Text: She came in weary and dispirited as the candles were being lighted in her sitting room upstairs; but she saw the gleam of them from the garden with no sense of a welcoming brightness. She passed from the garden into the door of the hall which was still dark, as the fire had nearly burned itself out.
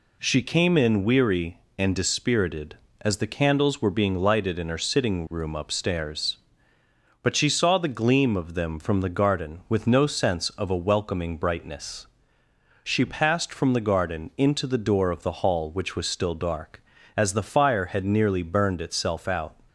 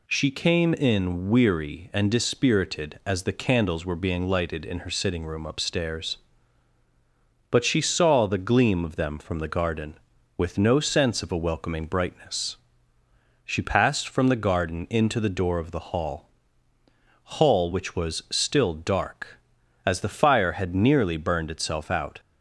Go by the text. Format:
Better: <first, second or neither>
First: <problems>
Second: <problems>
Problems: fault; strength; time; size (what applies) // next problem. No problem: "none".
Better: first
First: none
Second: says "hall" twice; at 17.3 s